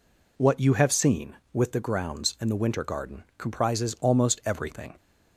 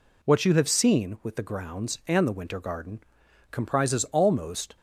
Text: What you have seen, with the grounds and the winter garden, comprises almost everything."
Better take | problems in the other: first | stops before "everything"; at 4.7 s

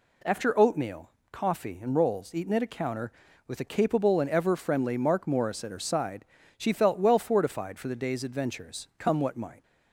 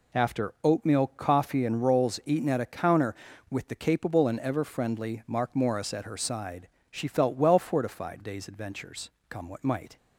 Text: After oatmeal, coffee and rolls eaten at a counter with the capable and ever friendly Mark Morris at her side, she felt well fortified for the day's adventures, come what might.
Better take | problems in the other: first | skips "for the"; at 8.2 s

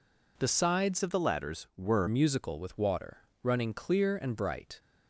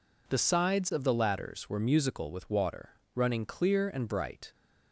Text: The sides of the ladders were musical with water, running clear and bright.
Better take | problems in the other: second | changes voice from "of" to "were"; from 1.0 to 2.0 s; 1.0 s long

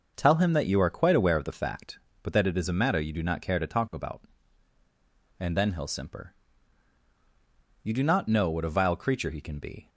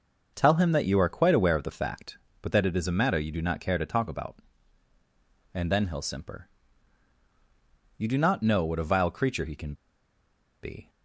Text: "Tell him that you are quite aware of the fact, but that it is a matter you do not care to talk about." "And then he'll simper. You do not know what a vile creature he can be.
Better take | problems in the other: first | pauses between "can" and "be"; noticeable; at 9.7 s; 0.87 s long

